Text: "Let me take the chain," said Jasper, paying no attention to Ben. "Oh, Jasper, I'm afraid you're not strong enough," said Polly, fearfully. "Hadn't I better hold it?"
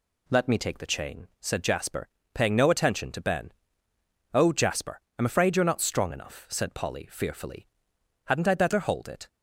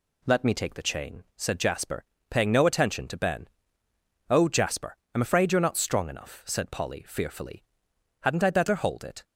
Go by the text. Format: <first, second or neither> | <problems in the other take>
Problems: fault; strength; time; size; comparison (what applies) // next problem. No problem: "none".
neither | none